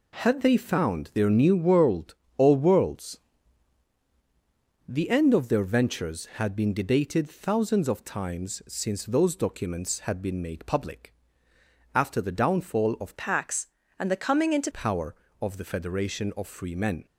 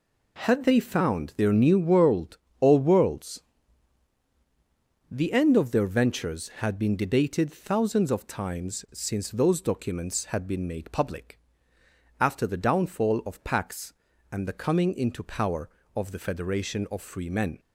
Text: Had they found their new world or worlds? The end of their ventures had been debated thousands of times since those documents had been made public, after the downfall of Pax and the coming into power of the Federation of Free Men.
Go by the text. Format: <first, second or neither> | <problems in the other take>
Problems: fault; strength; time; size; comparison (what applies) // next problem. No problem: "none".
second | changes voice from "Pax" to "into"; from 13.1 to 14.7 s; 1.6 s long